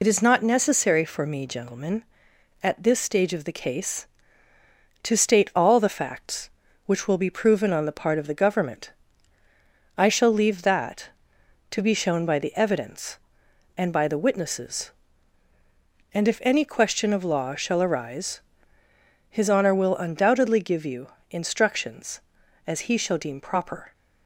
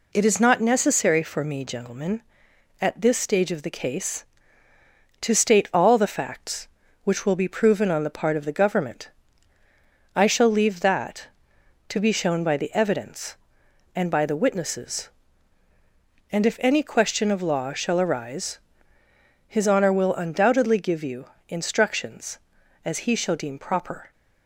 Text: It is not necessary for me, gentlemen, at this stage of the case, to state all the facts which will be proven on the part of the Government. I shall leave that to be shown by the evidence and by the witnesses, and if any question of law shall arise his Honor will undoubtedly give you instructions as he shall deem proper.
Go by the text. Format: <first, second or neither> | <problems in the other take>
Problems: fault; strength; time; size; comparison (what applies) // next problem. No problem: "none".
second | loses the start of "It"; at 0.0 s; 60 ms // pauses between "arise" and "his"; noticeable; at 18.3 s; 0.90 s long; noticeable in the second // pauses between "you" and "instructions"; slight; at 21.0 s; 0.22 s long; slight in the second